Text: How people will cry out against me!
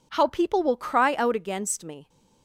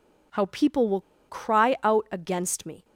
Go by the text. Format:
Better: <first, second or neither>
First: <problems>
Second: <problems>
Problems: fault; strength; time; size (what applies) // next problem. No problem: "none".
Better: first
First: none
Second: pauses between "will" and "cry"; slight; at 0.9 s; 0.29 s long